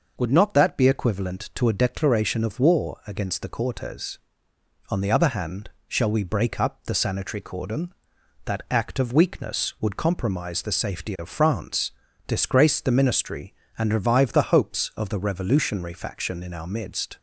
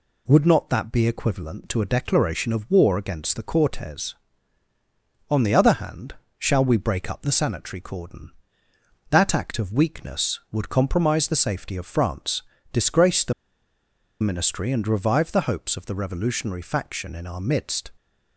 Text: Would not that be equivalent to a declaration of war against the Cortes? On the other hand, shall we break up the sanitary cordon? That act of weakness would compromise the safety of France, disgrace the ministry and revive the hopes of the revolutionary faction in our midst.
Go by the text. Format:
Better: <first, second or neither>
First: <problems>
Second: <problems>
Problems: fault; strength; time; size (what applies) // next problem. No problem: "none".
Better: first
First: none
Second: pauses between "the" and "ministry"; noticeable; at 13.3 s; 0.90 s long